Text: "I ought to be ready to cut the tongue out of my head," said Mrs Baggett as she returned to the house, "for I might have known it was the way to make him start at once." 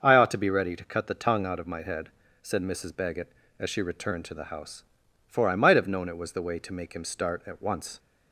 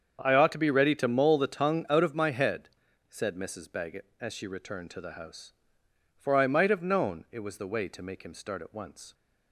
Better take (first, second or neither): first